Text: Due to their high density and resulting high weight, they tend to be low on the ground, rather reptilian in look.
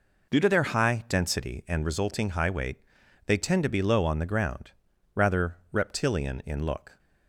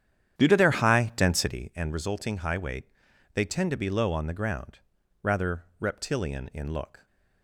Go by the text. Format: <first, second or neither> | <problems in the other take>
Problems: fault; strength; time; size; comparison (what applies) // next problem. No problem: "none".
first | starts louder than the rest; strong; until 1.7 s; 9.5 dB // pauses between "rather" and "reptilian"; slight; at 5.6 s; 0.16 s long; slight in the first